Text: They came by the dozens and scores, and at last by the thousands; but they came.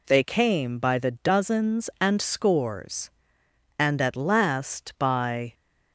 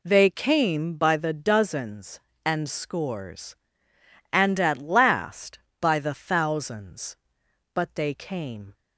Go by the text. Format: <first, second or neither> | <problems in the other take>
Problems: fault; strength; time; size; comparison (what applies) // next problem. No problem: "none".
second | stops before "the thousands but they came"; at 5.5 s